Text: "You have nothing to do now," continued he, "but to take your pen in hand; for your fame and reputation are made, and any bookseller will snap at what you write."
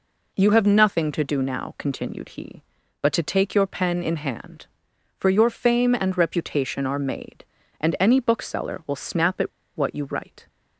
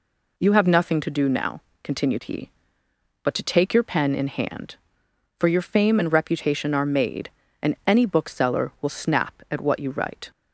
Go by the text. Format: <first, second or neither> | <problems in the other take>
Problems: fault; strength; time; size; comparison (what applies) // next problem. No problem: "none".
second | pauses between "at" and "what"; slight; at 9.5 s; 0.27 s long